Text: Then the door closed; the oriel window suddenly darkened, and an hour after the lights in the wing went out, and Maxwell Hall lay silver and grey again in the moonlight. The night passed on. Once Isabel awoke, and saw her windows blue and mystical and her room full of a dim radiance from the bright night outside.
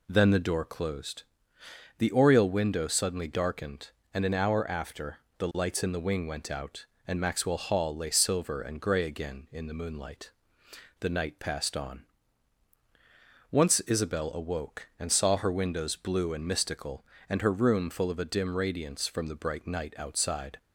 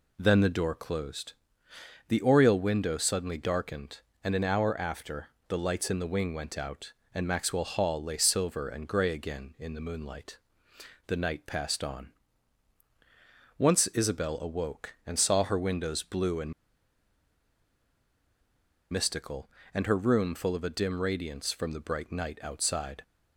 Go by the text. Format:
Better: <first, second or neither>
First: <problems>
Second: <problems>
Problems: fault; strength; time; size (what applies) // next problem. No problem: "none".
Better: first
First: pauses between "after" and "the"; slight; at 5.1 s; 0.22 s long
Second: pauses between "after" and "the"; slight; at 5.2 s; 0.22 s long // pauses between "and" and "mystical"; strong; at 16.5 s; 2.3 s long